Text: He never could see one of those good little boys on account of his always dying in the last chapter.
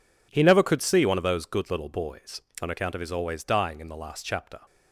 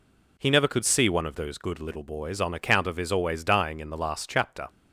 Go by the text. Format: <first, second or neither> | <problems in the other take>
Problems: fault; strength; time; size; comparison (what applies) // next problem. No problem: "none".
second | gets quieter; strong; throughout; 11.5 dB